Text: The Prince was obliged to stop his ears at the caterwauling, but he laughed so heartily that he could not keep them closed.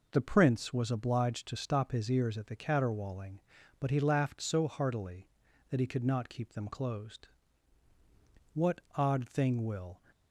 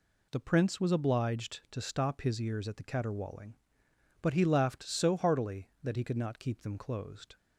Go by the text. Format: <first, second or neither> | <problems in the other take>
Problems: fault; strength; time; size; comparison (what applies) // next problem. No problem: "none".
second | goes on to say "What odd thing will"; from 8.5 s on; 1.4 s long